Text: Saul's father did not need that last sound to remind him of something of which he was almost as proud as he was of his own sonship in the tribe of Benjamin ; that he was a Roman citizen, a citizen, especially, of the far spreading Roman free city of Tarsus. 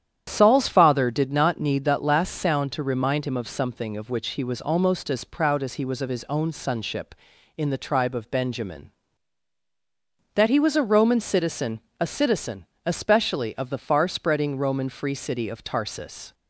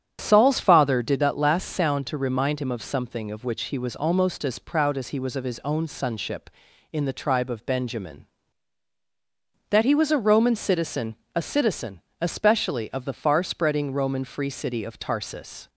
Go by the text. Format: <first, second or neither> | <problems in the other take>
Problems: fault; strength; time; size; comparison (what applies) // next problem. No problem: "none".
first | starts louder than the rest; strong; until 1.2 s; 8.5 dB; strong in the first // skips "not need"; at 1.2 s